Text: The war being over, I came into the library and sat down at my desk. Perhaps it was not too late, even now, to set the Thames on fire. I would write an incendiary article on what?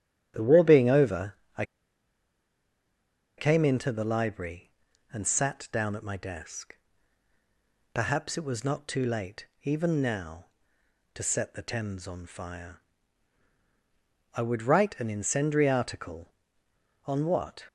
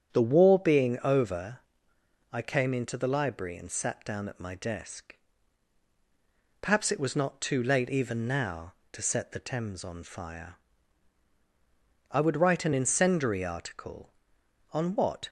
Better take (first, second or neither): second